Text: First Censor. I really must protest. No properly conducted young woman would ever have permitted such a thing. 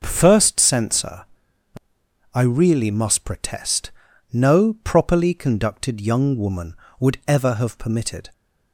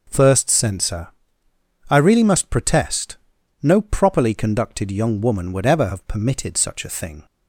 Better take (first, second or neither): second